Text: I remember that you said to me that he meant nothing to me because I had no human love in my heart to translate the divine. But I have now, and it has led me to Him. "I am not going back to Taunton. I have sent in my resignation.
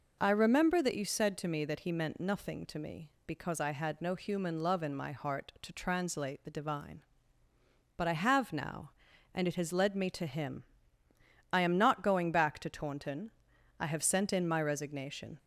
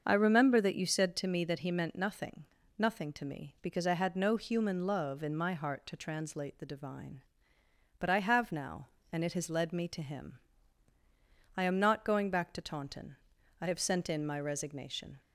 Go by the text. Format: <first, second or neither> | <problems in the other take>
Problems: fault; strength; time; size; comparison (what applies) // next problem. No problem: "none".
first | starts louder than the rest; until 1.0 s; 6.5 dB // says "nothing" twice; at 2.7 s